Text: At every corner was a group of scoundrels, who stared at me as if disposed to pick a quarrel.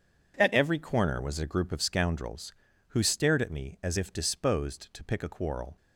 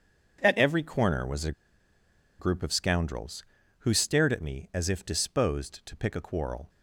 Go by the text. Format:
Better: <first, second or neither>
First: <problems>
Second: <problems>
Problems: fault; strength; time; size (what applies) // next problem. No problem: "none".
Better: first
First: none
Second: pauses between "a" and "group"; noticeable; at 1.5 s; 0.87 s long